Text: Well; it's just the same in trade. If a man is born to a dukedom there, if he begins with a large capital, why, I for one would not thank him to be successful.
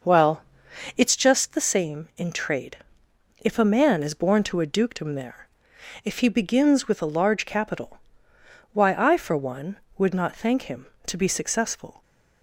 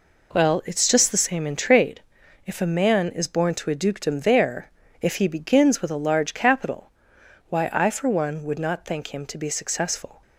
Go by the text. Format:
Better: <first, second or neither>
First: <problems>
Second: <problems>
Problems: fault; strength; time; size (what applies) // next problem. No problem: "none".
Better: second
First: starts louder than the rest; noticeable; until 1.2 s; 6 dB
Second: none